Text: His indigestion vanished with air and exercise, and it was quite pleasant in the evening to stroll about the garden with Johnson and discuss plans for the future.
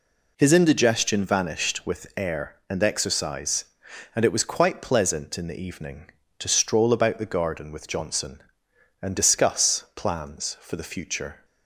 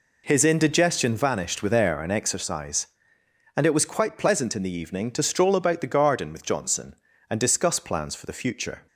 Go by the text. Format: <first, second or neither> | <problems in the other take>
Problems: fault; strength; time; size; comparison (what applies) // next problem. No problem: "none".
neither | none